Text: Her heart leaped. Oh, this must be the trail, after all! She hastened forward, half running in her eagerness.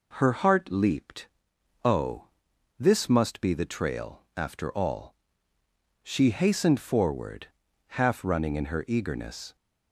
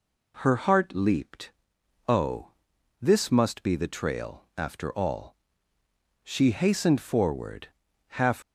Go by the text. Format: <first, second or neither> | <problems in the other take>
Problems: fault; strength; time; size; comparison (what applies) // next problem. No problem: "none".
first | stops before "running in her eagerness"; at 8.4 s